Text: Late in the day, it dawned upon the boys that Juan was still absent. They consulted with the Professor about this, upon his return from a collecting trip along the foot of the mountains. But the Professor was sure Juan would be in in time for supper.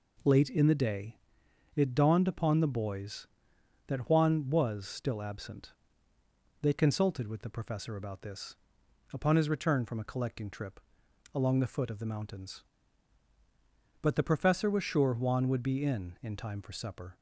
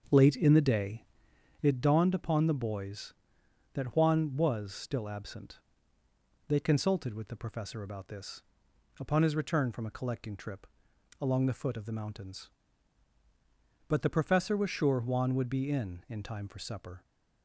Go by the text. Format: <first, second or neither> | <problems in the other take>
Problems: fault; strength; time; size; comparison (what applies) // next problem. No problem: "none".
first | starts louder than the rest; until 1.9 s; 7 dB // pauses between "trip" and "along"; noticeable; at 10.6 s; 0.54 s long; noticeable in the first